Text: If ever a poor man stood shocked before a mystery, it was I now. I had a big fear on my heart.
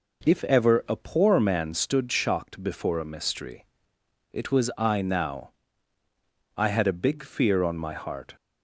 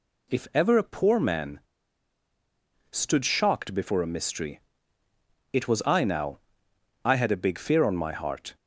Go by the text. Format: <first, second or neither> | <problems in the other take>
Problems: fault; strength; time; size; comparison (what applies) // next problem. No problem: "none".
first | pauses between "man" and "stood"; strong; at 1.5 s; 1.3 s long